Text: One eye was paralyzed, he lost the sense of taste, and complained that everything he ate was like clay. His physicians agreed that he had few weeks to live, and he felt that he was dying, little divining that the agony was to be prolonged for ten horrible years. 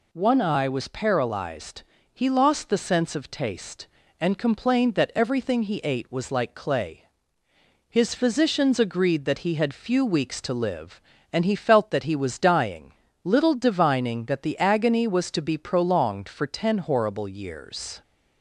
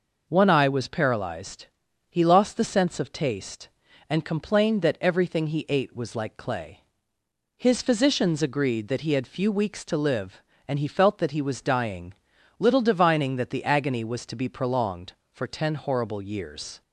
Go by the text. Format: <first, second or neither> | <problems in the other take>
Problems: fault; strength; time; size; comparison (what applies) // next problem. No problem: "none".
neither | none